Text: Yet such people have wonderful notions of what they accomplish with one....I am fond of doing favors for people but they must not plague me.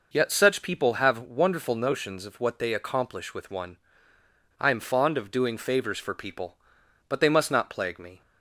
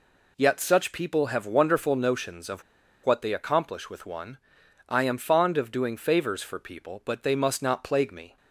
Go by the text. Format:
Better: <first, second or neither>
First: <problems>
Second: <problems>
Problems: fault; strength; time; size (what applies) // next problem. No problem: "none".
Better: first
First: none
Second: pauses between "of" and "what"; at 2.6 s; 0.41 s long